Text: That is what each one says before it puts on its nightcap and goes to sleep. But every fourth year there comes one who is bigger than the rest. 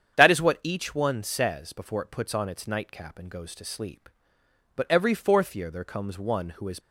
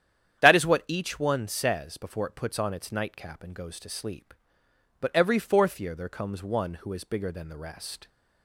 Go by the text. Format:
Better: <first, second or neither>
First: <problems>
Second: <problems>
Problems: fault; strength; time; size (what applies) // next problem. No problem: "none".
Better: second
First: starts louder than the rest; strong; until 1.1 s; 8.5 dB // stops before "bigger than the rest"; at 6.7 s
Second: starts louder than the rest; strong; until 1.4 s; 9.5 dB